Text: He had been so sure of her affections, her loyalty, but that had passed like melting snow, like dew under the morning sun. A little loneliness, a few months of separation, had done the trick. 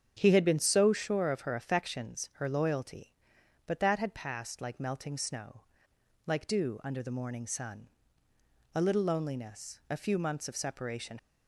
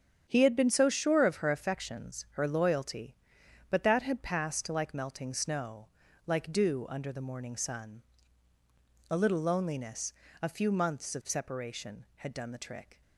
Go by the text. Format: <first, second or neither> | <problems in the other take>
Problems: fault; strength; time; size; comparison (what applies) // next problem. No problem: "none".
second | starts louder than the rest; strong; until 1.1 s; 7.5 dB; strong in the second // stops before "had done the trick"; at 11.1 s